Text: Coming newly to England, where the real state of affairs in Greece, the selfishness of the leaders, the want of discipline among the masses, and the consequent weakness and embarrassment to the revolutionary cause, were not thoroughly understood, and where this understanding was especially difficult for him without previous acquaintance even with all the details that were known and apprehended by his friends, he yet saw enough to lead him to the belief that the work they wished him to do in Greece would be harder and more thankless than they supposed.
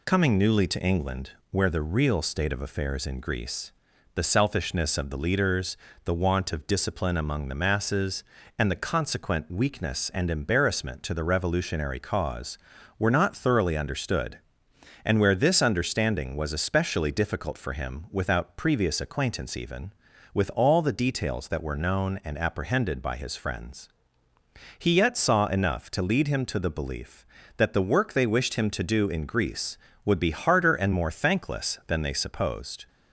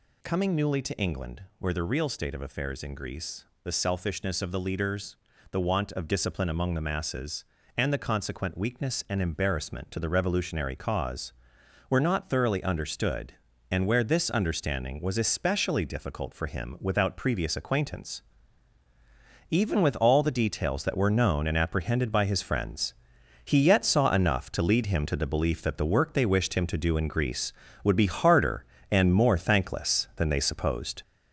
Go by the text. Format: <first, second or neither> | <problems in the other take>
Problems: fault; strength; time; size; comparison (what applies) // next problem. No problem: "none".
first | gets louder; noticeable; throughout; 5 dB // pauses between "acquaintance" and "even"; strong; at 18.2 s; 1.3 s long